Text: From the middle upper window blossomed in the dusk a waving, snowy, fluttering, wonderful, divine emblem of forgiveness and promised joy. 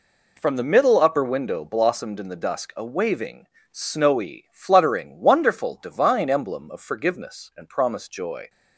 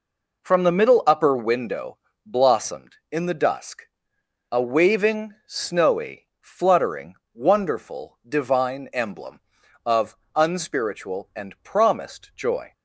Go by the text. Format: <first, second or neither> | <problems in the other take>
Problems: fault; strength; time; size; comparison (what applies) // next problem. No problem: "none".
first | pauses between "window" and "blossomed"; slight; at 1.9 s; 0.26 s long // pauses between "dusk" and "a"; noticeable; at 3.8 s; 0.64 s long // says "unspiritual" for "forgiveness"; at 10.3 s